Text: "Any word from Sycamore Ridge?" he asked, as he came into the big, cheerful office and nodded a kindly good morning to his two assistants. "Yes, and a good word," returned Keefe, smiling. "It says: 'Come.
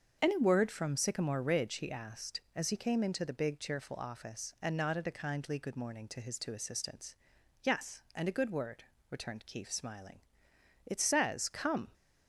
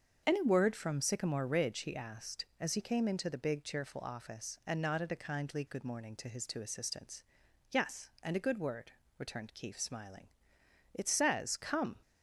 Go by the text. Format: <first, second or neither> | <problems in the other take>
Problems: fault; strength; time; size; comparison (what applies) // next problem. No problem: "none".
neither | starts louder than the rest; the same in both